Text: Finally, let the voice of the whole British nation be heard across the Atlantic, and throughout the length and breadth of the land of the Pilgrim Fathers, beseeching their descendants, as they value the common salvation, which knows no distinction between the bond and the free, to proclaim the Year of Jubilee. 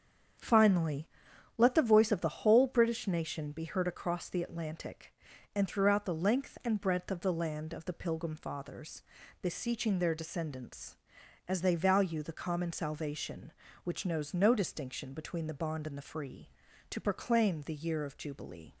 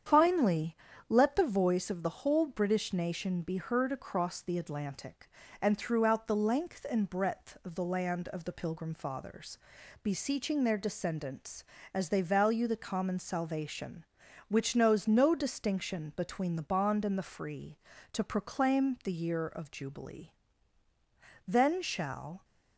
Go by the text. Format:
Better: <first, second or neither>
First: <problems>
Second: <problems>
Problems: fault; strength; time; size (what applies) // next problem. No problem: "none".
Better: first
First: starts louder than the rest; strong; until 1.9 s; 7.5 dB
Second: starts louder than the rest; strong; until 1.4 s; 8.5 dB // goes on to say "Then shall"; noticeable; from 21.4 s on; 0.96 s long